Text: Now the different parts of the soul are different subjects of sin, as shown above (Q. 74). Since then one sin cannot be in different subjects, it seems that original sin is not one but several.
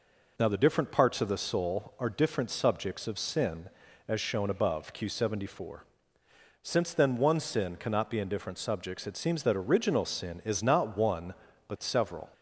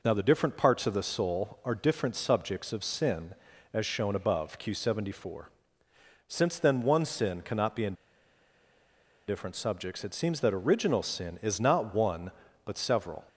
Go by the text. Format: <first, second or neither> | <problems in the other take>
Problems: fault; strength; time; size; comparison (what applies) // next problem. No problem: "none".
first | pauses between "in" and "different"; strong; at 7.9 s; 1.3 s long